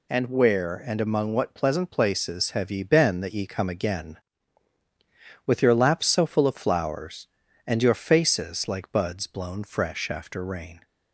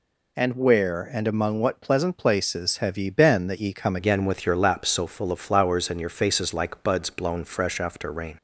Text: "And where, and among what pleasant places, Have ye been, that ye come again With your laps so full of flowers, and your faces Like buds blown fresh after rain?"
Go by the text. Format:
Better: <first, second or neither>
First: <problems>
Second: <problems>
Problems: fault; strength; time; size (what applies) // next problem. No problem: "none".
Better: first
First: none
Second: changes voice at "again"; from 3.9 s on; 4.4 s long